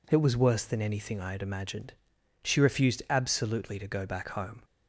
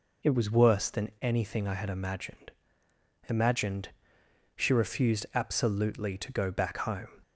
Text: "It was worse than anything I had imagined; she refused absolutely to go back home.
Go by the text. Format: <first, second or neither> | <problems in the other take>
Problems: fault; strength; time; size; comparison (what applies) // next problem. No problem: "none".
first | says "imagined" twice; at 3.2 s